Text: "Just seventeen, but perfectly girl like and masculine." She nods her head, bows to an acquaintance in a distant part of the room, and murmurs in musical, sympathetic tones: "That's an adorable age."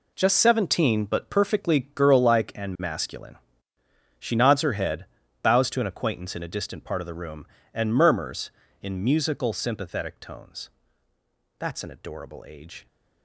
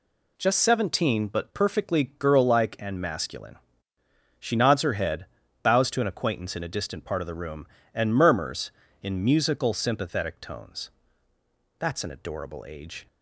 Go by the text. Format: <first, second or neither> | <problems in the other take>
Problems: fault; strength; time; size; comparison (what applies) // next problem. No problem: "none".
second | gets quieter; strong; throughout; 12.5 dB